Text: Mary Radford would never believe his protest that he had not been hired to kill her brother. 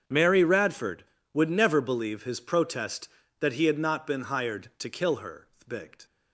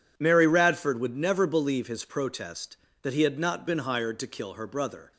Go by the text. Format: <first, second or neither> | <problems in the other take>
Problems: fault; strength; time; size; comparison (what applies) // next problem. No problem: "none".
second | starts louder than the rest; until 1.3 s; 7 dB // says "thbigt" for "brother"; at 5.6 s